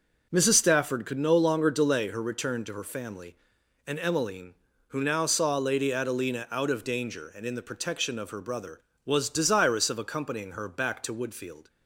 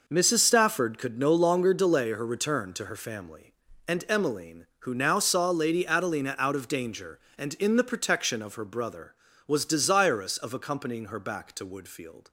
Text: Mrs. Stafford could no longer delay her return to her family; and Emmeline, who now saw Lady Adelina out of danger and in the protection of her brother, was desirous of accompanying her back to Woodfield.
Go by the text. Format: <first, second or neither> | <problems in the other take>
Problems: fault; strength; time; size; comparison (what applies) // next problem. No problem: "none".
neither | none